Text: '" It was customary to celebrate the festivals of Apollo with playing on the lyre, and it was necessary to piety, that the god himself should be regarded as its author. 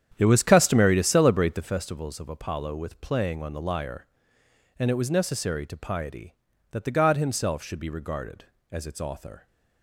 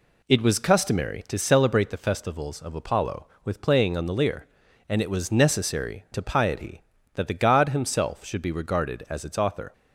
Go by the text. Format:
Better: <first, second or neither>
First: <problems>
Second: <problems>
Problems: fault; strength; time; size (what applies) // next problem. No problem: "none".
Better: second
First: starts louder than the rest; strong; until 1.7 s; 9 dB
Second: none